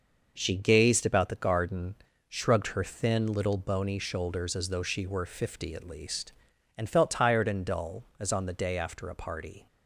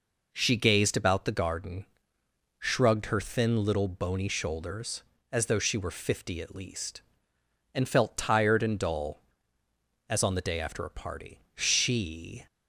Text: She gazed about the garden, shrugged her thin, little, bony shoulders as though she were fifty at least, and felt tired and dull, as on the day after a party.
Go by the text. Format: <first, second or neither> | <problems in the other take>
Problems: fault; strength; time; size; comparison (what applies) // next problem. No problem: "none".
first | goes on to say "She"; noticeable; from 11.5 s on; 0.92 s long